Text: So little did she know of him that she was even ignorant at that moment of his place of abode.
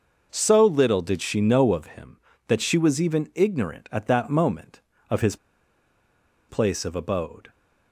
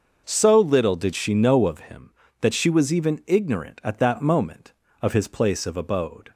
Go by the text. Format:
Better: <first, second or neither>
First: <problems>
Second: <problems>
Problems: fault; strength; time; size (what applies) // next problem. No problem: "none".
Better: second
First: pauses between "his" and "place"; at 5.3 s; 1.1 s long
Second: none